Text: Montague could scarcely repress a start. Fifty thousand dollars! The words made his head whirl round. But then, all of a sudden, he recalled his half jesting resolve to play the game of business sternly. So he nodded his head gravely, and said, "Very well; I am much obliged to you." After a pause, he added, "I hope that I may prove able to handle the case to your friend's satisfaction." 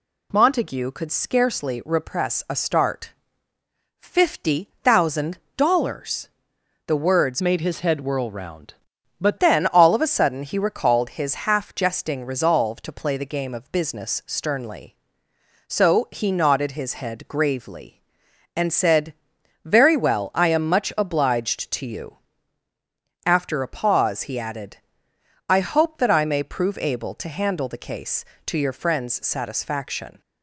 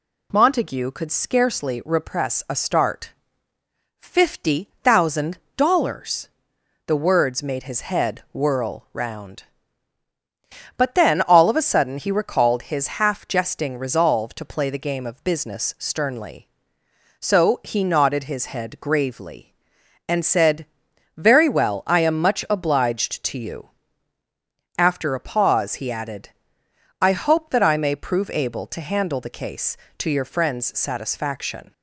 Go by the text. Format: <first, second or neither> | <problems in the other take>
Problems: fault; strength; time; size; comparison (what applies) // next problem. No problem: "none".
second | pauses between "thousand" and "dollars"; slight; at 5.3 s; 0.20 s long; slight in the second // changes voice from "made" to "But"; from 7.4 to 9.3 s; 1.9 s long